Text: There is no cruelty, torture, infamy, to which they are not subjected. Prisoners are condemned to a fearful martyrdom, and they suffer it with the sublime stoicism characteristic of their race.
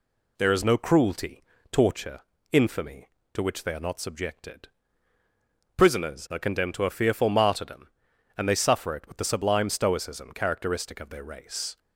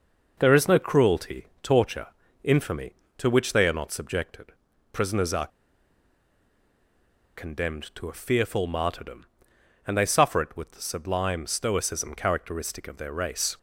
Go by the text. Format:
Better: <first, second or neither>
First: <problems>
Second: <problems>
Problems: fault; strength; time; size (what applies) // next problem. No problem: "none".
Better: first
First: none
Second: pauses between "are" and "condemned"; strong; at 5.4 s; 1.8 s long